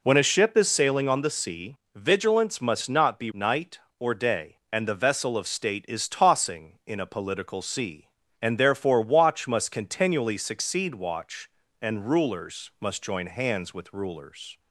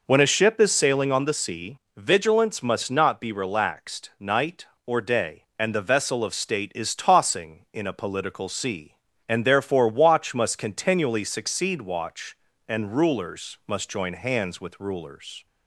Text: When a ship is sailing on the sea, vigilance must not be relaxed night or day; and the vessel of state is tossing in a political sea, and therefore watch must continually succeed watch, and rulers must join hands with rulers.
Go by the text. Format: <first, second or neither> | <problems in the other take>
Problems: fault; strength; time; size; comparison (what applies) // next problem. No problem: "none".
second | skips "relaxed"; at 3.3 s